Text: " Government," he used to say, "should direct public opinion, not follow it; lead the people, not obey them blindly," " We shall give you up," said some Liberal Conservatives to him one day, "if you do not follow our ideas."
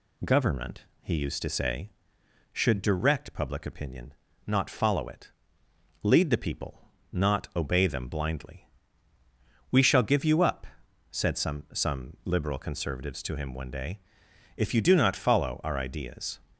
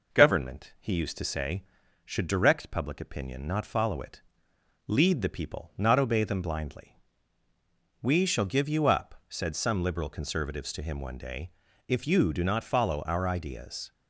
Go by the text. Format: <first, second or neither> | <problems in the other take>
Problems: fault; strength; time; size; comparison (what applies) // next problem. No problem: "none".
second | says "some" twice; at 11.7 s